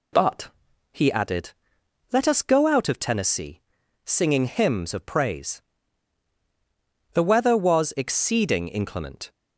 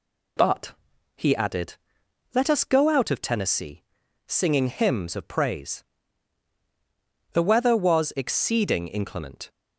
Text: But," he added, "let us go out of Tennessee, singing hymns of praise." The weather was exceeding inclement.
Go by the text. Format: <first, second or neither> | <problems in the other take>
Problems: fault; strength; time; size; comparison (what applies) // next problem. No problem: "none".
neither | none